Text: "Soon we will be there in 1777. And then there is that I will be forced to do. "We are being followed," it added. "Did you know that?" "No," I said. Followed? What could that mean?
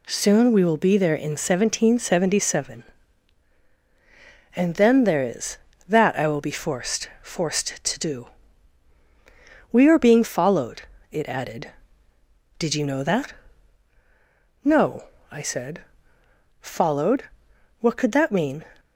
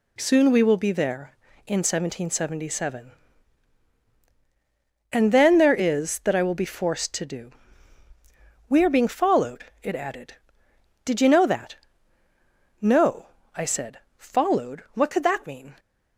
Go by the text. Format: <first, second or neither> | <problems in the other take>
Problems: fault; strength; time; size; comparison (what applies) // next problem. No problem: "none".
second | says "forced" twice; at 7.2 s